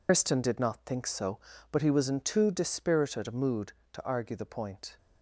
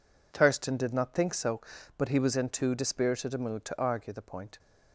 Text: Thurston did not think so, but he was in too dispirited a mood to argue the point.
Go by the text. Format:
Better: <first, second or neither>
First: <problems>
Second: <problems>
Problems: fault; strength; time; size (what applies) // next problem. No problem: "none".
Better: second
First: loses the start of "Thurston"; at 0.0 s; 145 ms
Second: none